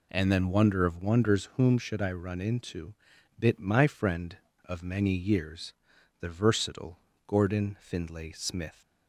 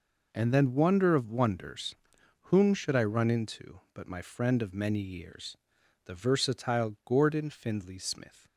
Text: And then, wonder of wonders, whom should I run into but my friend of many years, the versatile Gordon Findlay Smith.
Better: second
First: says "bit" for "but"; at 3.3 s // pauses between "versatile" and "Gordon"; slight; at 6.9 s; 0.28 s long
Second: none

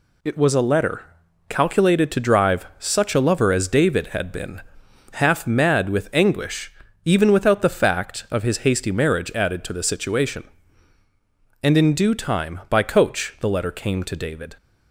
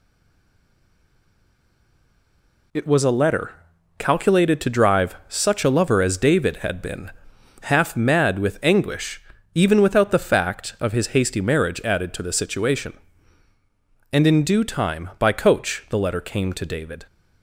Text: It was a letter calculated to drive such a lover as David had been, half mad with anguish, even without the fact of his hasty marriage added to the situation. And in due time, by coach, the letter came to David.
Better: first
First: pauses between "letter" and "calculated"; noticeable; at 1.0 s; 0.46 s long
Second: stays silent before the first word; strong; until 2.7 s; 2.7 s long // pauses between "letter" and "calculated"; noticeable; at 3.5 s; 0.46 s long

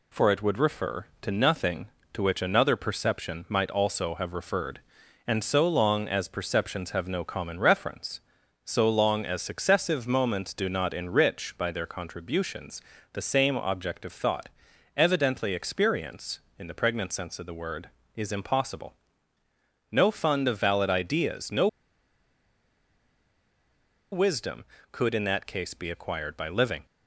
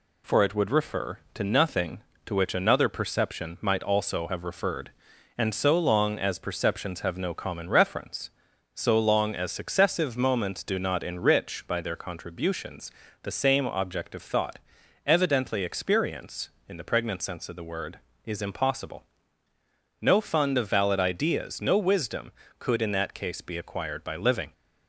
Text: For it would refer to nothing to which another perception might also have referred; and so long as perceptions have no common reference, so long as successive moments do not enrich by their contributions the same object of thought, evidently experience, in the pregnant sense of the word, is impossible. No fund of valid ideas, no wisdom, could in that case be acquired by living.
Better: second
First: pauses between "contributions" and "the"; slight; at 12.8 s; 0.30 s long // pauses between "no" and "wisdom"; strong; at 21.6 s; 2.4 s long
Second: pauses between "contributions" and "the"; slight; at 12.9 s; 0.30 s long

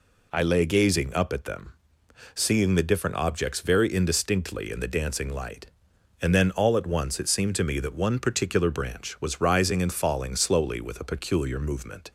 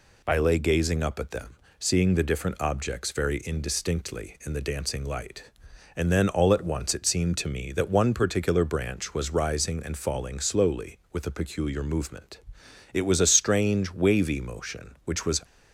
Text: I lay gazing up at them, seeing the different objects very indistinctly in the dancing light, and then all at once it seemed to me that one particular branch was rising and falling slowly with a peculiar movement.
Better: first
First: none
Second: goes on to say "It was a strange wavy motion which was"; strong; from 12.9 s on; 2.5 s long

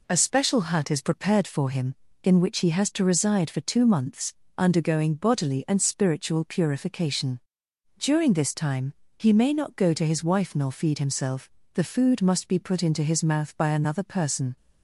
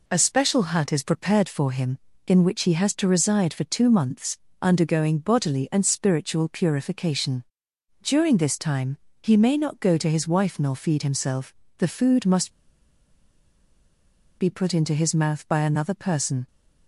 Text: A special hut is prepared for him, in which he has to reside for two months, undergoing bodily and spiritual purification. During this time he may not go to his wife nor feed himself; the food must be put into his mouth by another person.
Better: first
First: pauses between "time" and "he"; slight; at 8.9 s; 0.22 s long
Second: pauses between "time" and "he"; slight; at 8.9 s; 0.22 s long // pauses between "must" and "be"; strong; at 12.5 s; 1.8 s long

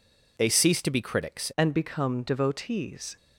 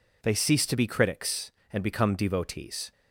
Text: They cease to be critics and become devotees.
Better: second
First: changes voice at "and"; from 1.5 s on; 1.6 s long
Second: none

